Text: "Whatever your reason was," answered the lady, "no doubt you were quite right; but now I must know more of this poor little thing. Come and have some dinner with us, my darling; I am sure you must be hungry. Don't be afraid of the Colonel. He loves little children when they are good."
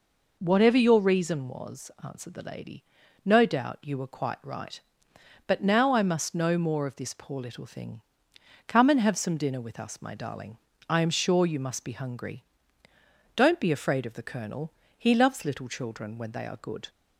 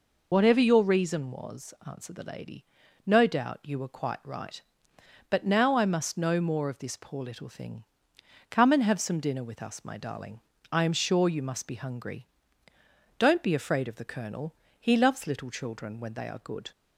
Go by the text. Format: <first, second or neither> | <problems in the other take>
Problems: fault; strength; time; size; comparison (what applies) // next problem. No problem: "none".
first | loses the start of "Whatever"; at 0.3 s; 90 ms